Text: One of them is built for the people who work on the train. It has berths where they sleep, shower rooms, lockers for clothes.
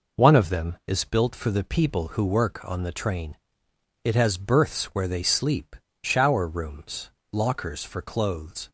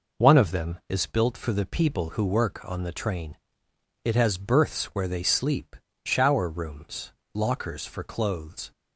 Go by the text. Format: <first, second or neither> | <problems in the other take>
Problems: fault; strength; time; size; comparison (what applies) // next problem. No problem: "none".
neither | none